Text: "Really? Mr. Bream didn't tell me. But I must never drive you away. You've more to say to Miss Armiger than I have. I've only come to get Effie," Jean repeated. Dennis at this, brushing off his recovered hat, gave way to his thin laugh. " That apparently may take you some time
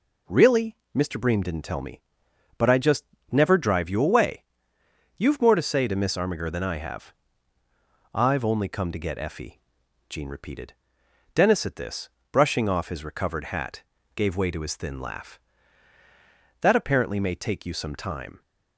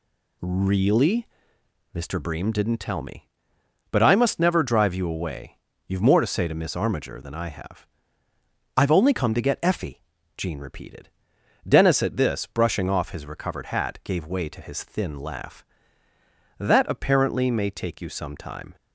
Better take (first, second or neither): second